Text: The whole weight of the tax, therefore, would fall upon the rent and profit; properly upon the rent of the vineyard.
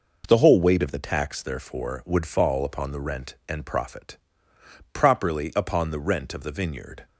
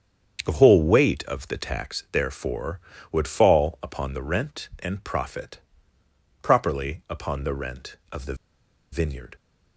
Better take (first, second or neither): first